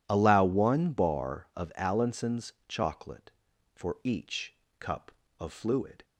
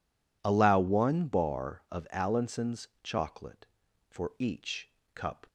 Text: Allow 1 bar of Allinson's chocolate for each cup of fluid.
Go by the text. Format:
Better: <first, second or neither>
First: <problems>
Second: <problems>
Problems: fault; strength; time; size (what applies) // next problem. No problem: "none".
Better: first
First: pauses between "Allinson's" and "chocolate"; slight; at 2.5 s; 0.16 s long // pauses between "each" and "cup"; slight; at 4.5 s; 0.24 s long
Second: pauses between "Allinson's" and "chocolate"; slight; at 2.8 s; 0.16 s long // pauses between "each" and "cup"; slight; at 4.8 s; 0.24 s long // stops before "of fluid"; at 5.4 s